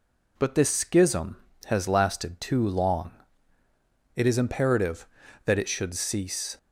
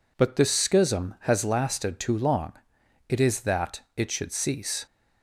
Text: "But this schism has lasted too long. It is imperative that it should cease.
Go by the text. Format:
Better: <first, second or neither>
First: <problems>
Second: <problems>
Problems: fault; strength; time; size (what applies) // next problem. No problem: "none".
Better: first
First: none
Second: skips "imperative"; at 3.4 s